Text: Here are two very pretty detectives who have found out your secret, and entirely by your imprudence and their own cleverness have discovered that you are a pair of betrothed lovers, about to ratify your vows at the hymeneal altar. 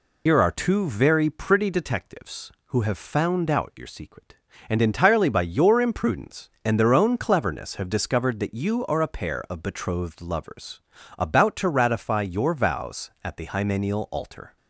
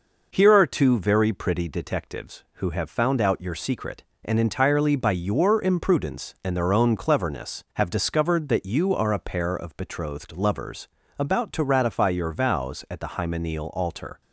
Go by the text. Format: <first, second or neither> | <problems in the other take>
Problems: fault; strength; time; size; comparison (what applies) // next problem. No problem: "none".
second | loses the start of "Here"; at 0.2 s; 75 ms